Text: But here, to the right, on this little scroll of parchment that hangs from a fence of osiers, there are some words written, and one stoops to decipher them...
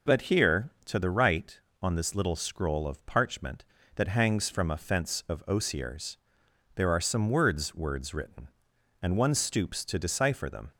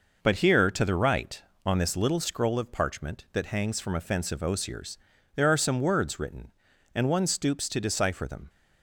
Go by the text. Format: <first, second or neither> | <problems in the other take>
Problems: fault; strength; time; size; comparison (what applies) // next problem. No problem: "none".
second | says "words" twice; at 7.7 s